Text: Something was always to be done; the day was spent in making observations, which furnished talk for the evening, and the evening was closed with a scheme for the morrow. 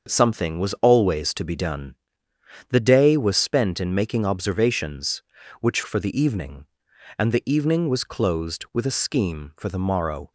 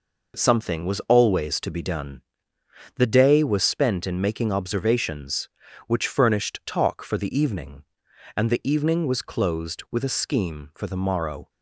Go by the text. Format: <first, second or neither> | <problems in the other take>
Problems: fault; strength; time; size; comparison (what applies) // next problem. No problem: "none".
second | starts louder than the rest; until 1.1 s; 6.5 dB // skips "furnished talk"; at 5.8 s